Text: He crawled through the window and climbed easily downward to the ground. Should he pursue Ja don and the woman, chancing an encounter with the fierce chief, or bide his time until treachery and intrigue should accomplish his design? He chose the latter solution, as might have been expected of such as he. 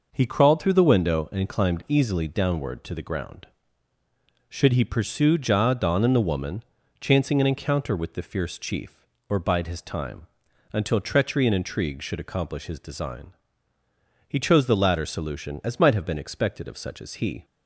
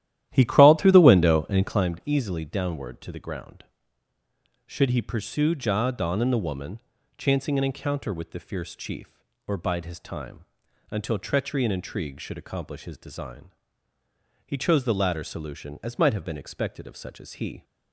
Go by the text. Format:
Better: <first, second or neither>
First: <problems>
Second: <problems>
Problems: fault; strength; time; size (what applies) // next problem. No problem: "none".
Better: first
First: pauses between "time" and "until"; noticeable; at 10.2 s; 0.46 s long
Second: starts louder than the rest; strong; until 1.9 s; 12.5 dB // pauses between "time" and "until"; noticeable; at 10.4 s; 0.46 s long